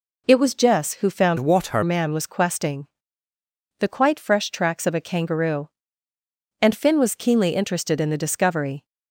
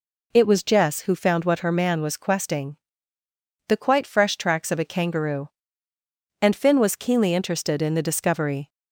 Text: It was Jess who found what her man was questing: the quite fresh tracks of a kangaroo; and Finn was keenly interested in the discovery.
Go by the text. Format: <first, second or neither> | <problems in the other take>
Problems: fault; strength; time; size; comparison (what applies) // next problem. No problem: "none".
second | changes voice from "what" to "her"; from 1.3 to 1.8 s; 0.5 s long